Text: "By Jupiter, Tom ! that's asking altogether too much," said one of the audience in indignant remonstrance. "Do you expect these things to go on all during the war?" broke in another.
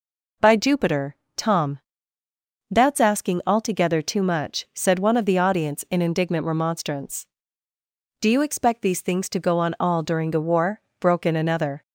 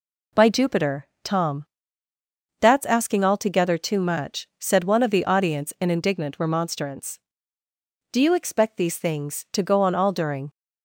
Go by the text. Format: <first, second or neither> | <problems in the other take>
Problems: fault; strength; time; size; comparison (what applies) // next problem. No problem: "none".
first | stops before "the war broke in another"; at 10.4 s